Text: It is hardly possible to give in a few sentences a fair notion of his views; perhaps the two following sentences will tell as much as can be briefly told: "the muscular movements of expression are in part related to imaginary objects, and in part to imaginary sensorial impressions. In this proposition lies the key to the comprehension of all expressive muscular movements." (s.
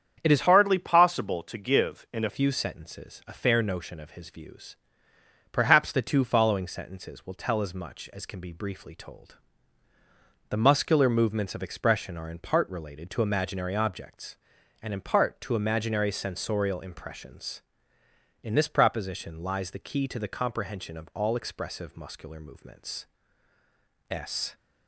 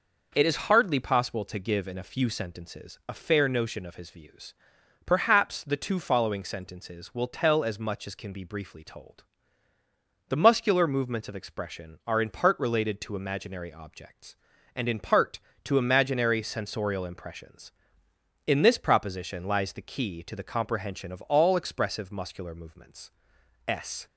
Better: second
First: starts louder than the rest; strong; until 1.2 s; 8 dB // changes voice from "hardly" to "a"; from 0.4 to 2.2 s; 1.8 s long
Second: none

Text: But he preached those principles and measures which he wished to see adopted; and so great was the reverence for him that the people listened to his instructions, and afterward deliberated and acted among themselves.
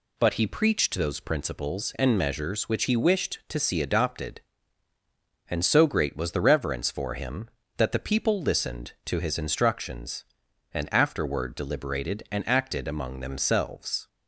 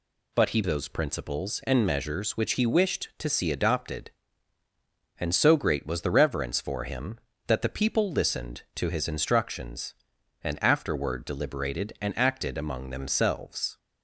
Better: first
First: none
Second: skips "preached"; at 0.6 s

